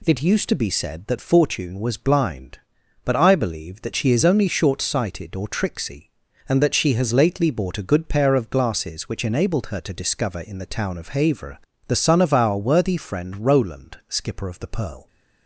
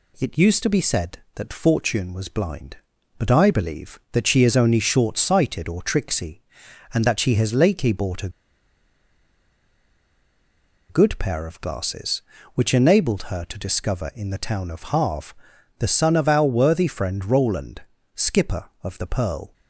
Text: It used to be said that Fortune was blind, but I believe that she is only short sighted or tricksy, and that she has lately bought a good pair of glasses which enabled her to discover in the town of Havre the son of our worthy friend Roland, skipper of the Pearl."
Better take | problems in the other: first | pauses between "a" and "good"; strong; at 8.2 s; 2.6 s long // pauses between "Havre" and "the"; at 15.3 s; 0.44 s long; slight in the first

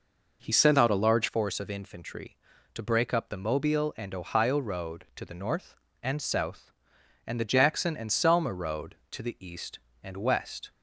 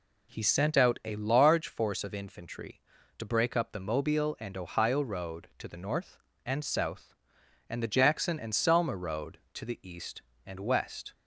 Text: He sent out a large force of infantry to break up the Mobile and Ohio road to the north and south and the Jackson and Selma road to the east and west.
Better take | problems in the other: second | changes voice from "sent" to "large"; from 0.5 to 1.2 s; 0.7 s long

